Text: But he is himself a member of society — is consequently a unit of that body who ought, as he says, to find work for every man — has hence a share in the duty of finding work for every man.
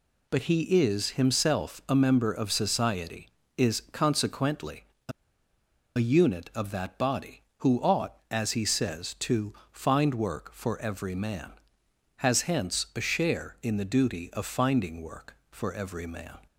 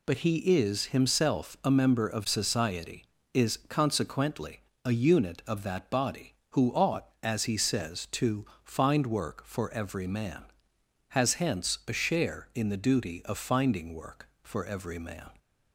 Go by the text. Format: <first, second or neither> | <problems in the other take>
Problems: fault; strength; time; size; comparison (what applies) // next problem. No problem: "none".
second | pauses between "consequently" and "a"; slight; at 4.8 s; 0.24 s long; slight in the second // pauses between "a" and "unit"; noticeable; at 5.1 s; 0.86 s long // pauses between "to" and "find"; slight; at 9.5 s; 0.20 s long; slight in the second